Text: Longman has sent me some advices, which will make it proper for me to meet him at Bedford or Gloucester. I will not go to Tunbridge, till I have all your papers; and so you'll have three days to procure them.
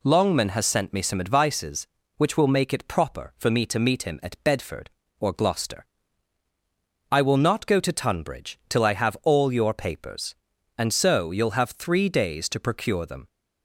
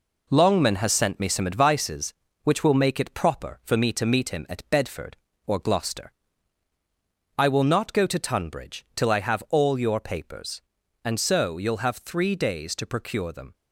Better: first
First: none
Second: gets quieter; noticeable; throughout; 5.5 dB

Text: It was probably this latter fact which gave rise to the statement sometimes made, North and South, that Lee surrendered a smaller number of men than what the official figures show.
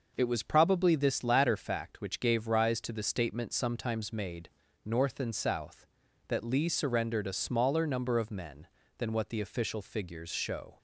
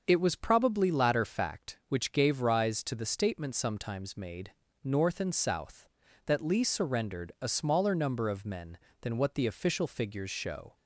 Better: first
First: none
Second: starts louder than the rest; until 1.0 s; 6.5 dB // skips "this"; at 0.9 s

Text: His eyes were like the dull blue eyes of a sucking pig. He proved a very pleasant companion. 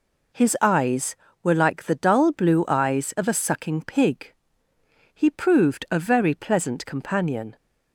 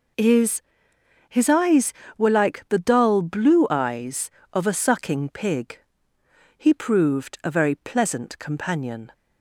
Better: first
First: none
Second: says "His" twice; at 1.3 s

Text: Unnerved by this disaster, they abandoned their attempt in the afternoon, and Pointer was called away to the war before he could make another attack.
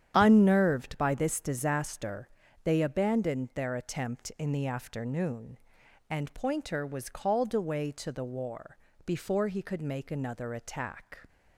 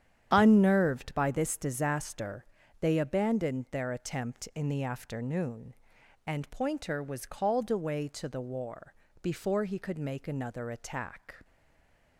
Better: first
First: starts louder than the rest; strong; until 1.1 s; 8.5 dB // pauses between "war" and "before"; slight; at 8.7 s; 0.28 s long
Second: starts louder than the rest; strong; until 1.3 s; 9 dB // pauses between "war" and "before"; slight; at 8.9 s; 0.28 s long // stays silent after the last word; slight; from 11.4 s on; 0.7 s long

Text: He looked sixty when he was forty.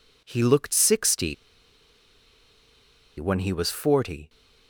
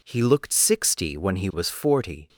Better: second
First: pauses between "sixty" and "when"; strong; at 1.3 s; 1.8 s long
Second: none

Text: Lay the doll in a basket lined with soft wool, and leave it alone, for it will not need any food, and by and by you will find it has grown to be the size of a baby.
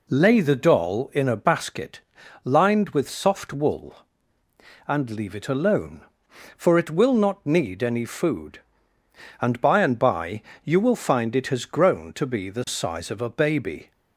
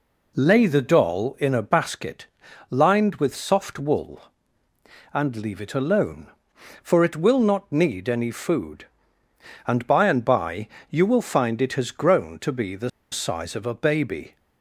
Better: first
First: pauses between "basket" and "lined"; at 2.0 s; 0.42 s long // pauses between "by" and "you"; slight; at 10.4 s; 0.24 s long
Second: pauses between "basket" and "lined"; at 2.2 s; 0.42 s long // pauses between "by" and "you"; slight; at 10.6 s; 0.24 s long // pauses between "the" and "size"; slight; at 12.8 s; 0.22 s long

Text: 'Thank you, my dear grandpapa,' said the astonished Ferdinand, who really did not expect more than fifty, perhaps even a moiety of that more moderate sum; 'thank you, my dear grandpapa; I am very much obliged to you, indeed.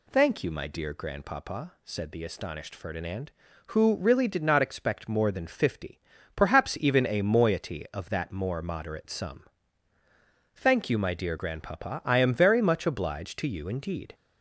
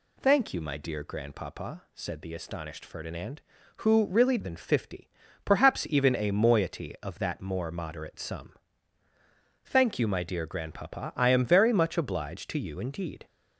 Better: first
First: none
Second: skips "did not expect more"; at 4.3 s

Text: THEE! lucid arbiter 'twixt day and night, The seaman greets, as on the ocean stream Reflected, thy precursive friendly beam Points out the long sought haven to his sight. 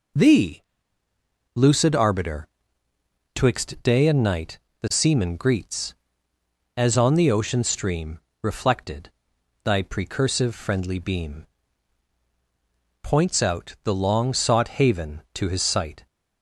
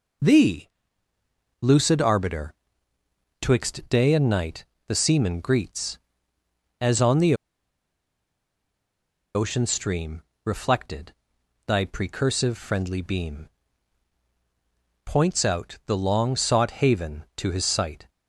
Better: first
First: pauses between "arbiter" and "twixt"; noticeable; at 2.4 s; 0.88 s long // pauses between "stream" and "Reflected"; slight; at 8.1 s; 0.22 s long // pauses between "beam" and "Points"; strong; at 11.4 s; 1.5 s long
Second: pauses between "arbiter" and "twixt"; noticeable; at 2.5 s; 0.88 s long // pauses between "the" and "ocean"; strong; at 7.3 s; 2.0 s long // pauses between "stream" and "Reflected"; slight; at 10.2 s; 0.22 s long // pauses between "beam" and "Points"; strong; at 13.4 s; 1.5 s long

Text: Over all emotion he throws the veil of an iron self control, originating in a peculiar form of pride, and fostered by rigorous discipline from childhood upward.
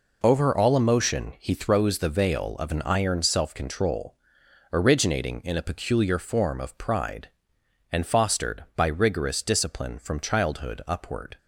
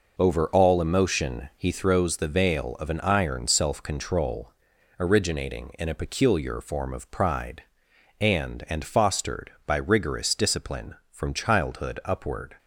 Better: first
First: none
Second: says "and" twice; at 8.6 s

